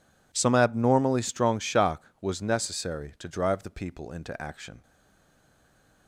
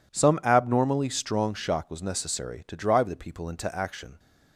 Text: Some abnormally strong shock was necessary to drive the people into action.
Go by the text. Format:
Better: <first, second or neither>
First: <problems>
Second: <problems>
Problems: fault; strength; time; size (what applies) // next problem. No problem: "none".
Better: second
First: stays silent after the last word; noticeable; from 4.8 s on; 1.2 s long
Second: none